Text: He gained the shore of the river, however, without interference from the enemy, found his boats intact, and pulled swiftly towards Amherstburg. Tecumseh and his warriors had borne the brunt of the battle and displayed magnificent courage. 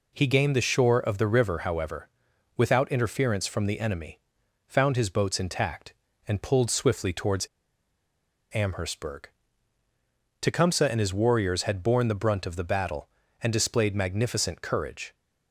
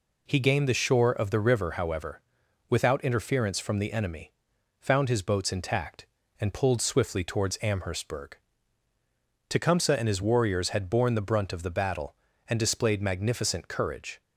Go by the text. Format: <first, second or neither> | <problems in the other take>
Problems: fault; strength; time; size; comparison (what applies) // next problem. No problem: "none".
second | pauses between "towards" and "Amherstburg"; at 7.4 s; 1.0 s long